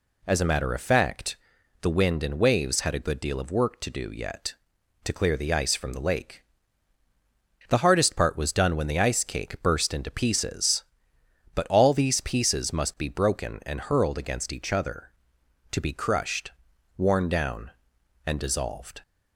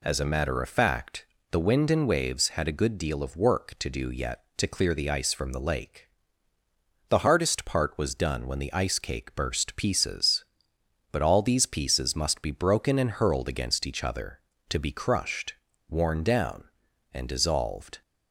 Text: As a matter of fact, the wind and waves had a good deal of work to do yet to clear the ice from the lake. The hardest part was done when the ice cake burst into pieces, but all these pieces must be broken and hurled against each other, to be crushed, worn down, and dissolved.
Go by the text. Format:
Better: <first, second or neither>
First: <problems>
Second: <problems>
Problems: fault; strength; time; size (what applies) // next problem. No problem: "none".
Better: first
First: none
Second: skips "into"; at 9.7 s